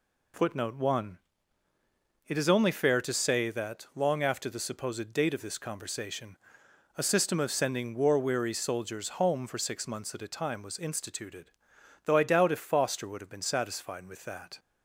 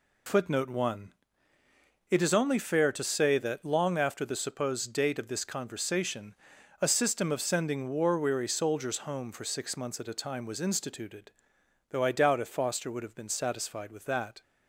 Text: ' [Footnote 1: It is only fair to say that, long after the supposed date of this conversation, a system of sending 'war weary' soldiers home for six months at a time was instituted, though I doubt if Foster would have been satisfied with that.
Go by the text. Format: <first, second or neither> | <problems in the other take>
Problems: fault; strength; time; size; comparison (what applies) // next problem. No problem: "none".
neither | none